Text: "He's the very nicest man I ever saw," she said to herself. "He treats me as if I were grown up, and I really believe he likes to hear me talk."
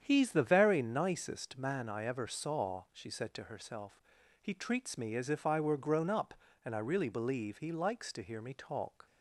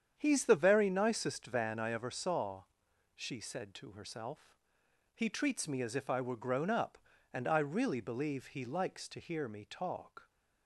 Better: first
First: starts louder than the rest; strong; until 1.0 s; 8.5 dB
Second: starts louder than the rest; strong; until 1.1 s; 8.5 dB // says "van" for "man"; at 1.4 s

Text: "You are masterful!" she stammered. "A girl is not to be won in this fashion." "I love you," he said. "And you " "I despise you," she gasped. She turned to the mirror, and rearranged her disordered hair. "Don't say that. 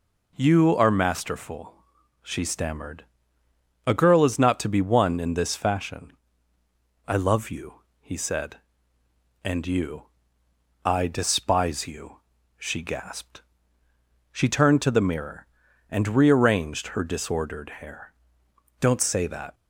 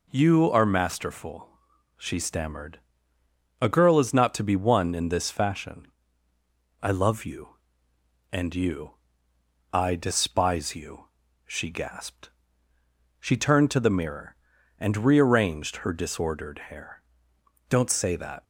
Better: first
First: none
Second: skips "he said"; at 7.9 s

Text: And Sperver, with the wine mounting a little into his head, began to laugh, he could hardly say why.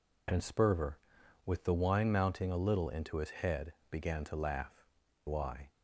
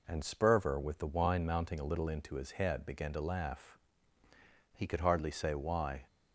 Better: second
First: skips "he could hardly say"; at 5.0 s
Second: none

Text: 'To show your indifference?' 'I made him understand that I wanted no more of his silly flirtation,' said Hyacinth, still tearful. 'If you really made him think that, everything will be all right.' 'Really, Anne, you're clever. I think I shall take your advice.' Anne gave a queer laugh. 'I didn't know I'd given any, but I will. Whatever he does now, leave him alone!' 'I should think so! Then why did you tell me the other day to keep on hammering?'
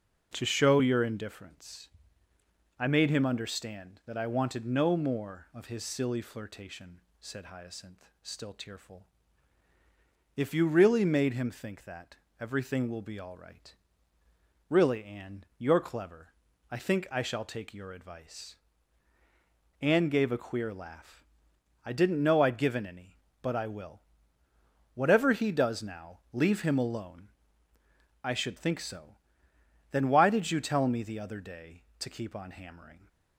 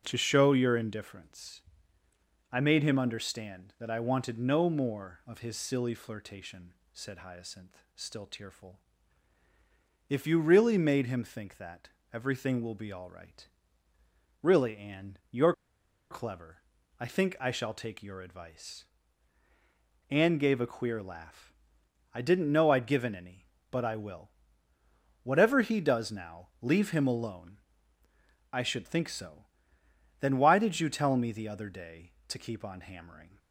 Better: first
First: none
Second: pauses between "you're" and "clever"; noticeable; at 15.5 s; 0.56 s long

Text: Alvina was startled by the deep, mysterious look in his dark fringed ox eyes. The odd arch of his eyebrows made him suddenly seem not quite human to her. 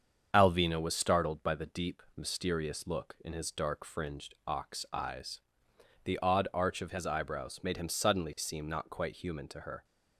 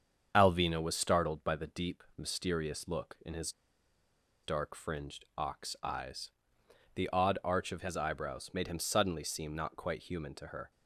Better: first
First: starts louder than the rest; strong; until 1.3 s; 7.5 dB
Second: starts louder than the rest; strong; until 1.3 s; 7.5 dB // pauses between "his" and "dark"; noticeable; at 3.5 s; 0.92 s long

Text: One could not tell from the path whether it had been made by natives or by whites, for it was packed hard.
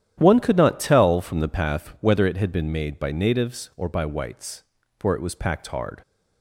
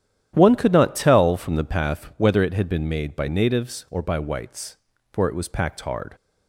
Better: neither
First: starts louder than the rest; strong; until 1.1 s; 10.5 dB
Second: starts louder than the rest; strong; until 1.3 s; 10.5 dB

